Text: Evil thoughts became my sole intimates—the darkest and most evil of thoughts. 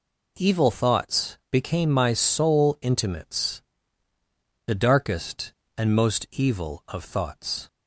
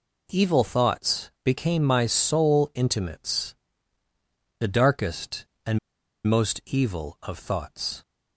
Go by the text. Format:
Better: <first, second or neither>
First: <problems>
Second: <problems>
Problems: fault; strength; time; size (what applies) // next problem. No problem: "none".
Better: first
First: none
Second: pauses between "and" and "most"; noticeable; at 5.7 s; 0.47 s long